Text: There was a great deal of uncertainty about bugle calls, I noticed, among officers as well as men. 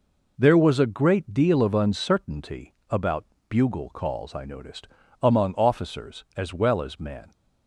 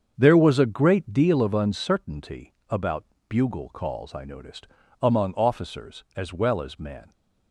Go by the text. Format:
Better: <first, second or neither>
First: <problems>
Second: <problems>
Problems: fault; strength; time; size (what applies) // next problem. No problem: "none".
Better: first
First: pauses between "uncertainty" and "about"; slight; at 2.7 s; 0.16 s long // pauses between "about" and "bugle"; slight; at 3.2 s; 0.24 s long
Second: starts louder than the rest; strong; until 1.4 s; 7 dB // pauses between "uncertainty" and "about"; slight; at 2.5 s; 0.16 s long // pauses between "about" and "bugle"; slight; at 3.0 s; 0.24 s long